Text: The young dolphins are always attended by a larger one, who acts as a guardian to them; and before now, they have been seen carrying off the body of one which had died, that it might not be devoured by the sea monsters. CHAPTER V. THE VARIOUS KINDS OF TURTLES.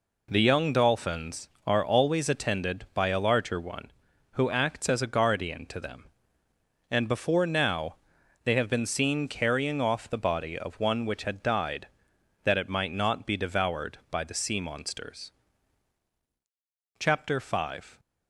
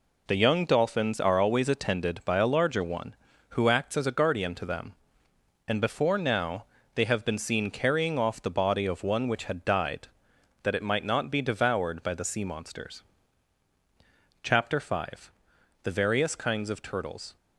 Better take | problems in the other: second | stops before "THE VARIOUS KINDS OF TURTLES"; at 17.9 s

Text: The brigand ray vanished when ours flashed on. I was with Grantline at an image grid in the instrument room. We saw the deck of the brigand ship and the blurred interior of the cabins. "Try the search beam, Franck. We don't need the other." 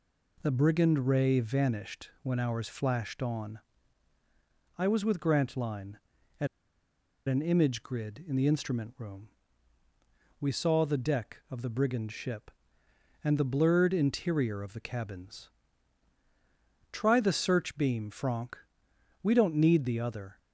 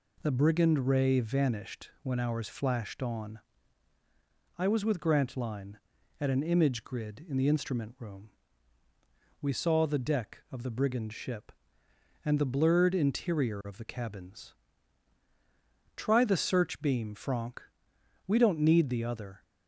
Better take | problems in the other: second | pauses between "at" and "an"; noticeable; at 6.4 s; 0.80 s long

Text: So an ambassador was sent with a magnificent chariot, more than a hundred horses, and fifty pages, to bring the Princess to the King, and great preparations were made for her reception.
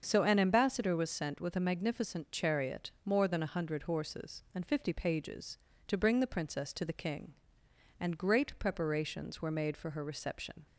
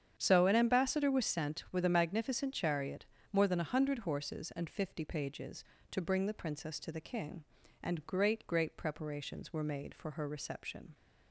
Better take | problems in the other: first | starts louder than the rest; strong; until 1.1 s; 8.5 dB; also in the first // says "great" twice; at 8.4 s

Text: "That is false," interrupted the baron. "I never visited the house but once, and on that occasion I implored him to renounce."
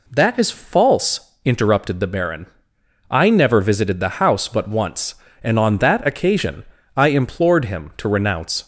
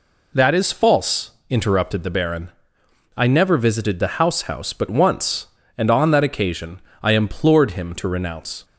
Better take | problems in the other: first | says "house" twice; at 4.4 s // pauses between "occasion" and "I"; slight; at 6.8 s; 0.22 s long; slight in the first

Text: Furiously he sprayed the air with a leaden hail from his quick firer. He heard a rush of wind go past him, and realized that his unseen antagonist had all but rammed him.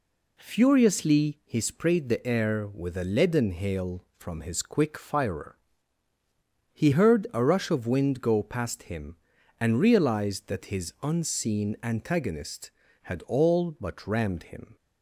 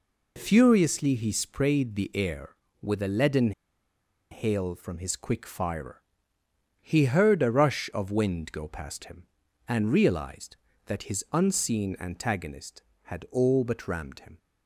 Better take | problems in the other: first | pauses between "leaden" and "hail"; noticeable; at 3.5 s; 0.80 s long

